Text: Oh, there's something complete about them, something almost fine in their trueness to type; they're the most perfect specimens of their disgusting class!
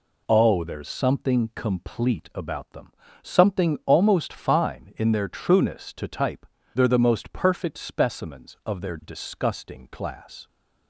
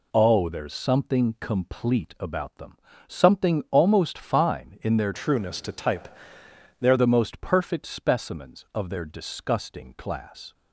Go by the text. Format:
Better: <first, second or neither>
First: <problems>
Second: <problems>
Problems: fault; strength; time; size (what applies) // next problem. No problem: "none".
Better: first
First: none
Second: changes voice from "trueness" to "they're"; from 5.1 to 6.9 s; 1.8 s long